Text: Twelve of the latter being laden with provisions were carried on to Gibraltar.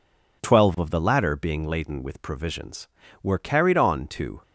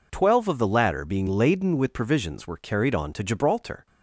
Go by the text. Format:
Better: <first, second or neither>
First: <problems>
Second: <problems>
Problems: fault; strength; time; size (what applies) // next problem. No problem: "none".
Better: second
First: stops before "Gibraltar"; at 4.4 s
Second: none